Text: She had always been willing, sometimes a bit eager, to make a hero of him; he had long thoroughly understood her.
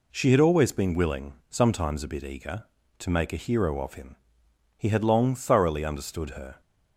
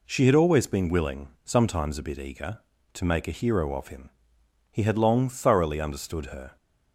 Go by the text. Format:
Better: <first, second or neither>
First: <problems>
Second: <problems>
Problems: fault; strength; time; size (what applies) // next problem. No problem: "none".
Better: neither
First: none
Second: none